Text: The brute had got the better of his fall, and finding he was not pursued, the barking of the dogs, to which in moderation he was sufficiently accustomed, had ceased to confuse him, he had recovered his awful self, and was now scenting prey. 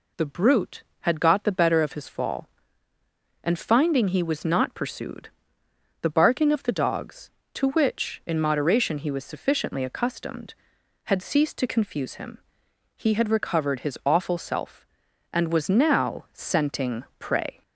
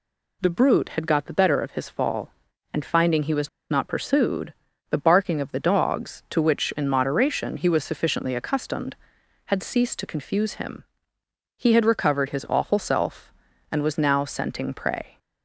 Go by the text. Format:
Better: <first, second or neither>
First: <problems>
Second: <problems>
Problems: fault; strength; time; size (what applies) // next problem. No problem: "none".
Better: first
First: none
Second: pauses between "was" and "not"; slight; at 3.4 s; 0.21 s long